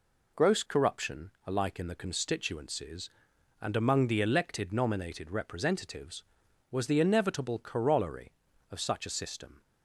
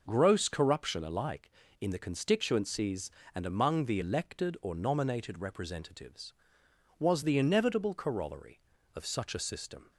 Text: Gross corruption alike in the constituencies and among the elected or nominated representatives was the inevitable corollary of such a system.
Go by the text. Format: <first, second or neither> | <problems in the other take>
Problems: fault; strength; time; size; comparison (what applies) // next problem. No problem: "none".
second | skips "or"; at 4.7 s